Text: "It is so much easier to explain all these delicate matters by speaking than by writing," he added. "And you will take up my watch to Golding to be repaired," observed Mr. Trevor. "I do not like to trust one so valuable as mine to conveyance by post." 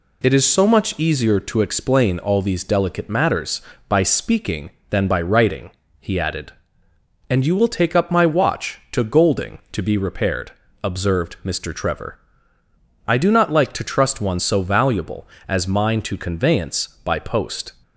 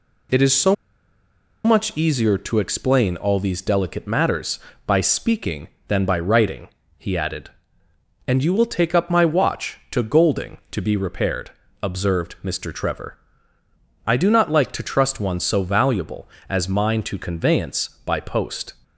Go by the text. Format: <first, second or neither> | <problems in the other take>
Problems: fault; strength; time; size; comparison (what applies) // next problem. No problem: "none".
first | pauses between "so" and "much"; noticeable; at 0.7 s; 0.90 s long